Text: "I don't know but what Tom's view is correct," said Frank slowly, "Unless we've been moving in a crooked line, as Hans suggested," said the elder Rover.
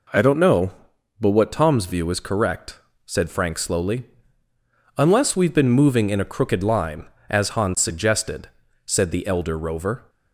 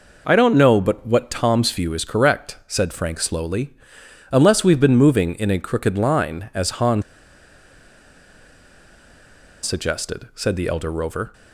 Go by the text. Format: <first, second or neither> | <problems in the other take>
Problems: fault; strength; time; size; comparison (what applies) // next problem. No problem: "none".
first | pauses between "Hans" and "suggested"; strong; at 7.0 s; 2.6 s long